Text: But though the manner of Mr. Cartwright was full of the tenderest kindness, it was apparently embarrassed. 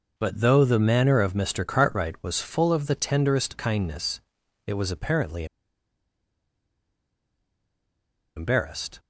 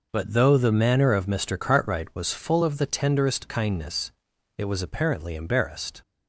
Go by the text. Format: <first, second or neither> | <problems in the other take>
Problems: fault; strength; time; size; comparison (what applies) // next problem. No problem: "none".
second | pauses between "apparently" and "embarrassed"; strong; at 5.4 s; 2.9 s long